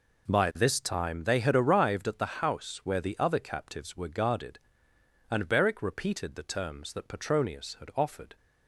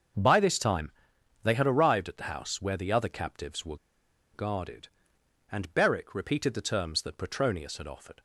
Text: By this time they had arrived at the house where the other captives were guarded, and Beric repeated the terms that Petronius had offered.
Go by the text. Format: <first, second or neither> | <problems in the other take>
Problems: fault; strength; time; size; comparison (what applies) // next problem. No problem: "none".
first | starts louder than the rest; until 1.7 s; 7 dB // pauses between "time" and "they"; noticeable; at 0.9 s; 0.52 s long // pauses between "were" and "guarded"; noticeable; at 3.7 s; 0.58 s long